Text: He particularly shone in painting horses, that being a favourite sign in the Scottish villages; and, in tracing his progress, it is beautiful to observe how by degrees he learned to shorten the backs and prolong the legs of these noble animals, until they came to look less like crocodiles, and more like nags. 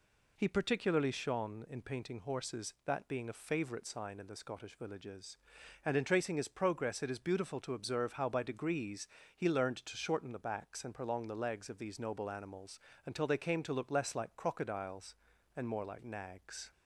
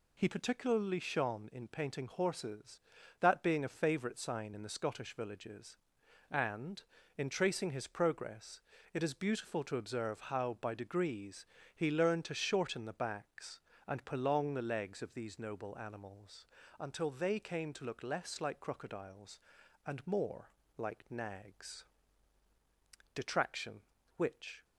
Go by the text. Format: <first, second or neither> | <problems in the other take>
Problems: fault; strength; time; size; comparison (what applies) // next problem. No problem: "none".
first | pauses between "degrees" and "he"; slight; at 11.4 s; 0.30 s long; slight in the first // pauses between "more" and "like"; slight; at 20.5 s; 0.28 s long // goes on to say "Detraction which"; from 23.1 s on; 1.5 s long